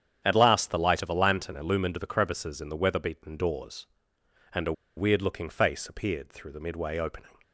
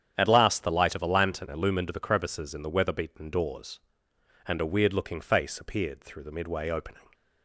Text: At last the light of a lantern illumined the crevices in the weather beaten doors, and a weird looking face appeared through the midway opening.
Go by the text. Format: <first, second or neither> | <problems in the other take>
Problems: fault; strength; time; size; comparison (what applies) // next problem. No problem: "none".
second | starts louder than the rest; strong; until 1.2 s; 9 dB; strong in the second // pauses between "a" and "weird"; slight; at 4.7 s; 0.24 s long